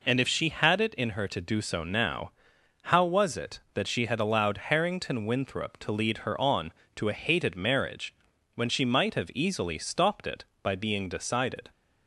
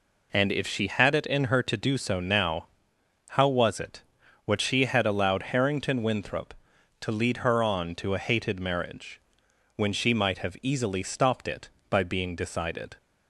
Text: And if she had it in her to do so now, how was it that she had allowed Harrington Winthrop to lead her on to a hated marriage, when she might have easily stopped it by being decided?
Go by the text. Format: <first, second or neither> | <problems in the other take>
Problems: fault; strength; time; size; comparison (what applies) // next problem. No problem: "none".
first | says "what" for "that"; at 4.4 s